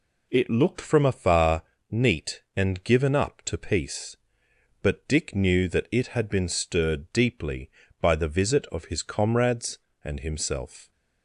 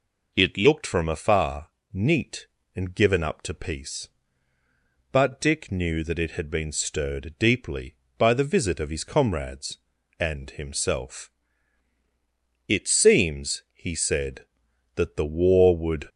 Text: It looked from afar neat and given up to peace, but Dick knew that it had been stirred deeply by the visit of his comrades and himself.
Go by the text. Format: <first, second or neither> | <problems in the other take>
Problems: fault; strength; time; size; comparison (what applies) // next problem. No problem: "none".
first | pauses between "afar" and "neat"; slight; at 1.6 s; 0.24 s long; slight in the first // goes on to say "It seems he said that the war would"; strong; from 12.6 s on; 3.4 s long